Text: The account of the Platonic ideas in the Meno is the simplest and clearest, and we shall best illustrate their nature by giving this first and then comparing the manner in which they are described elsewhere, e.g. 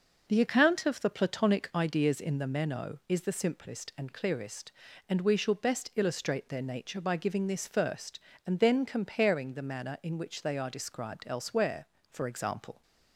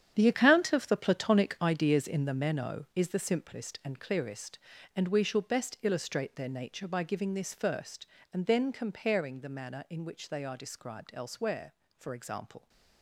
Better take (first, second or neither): first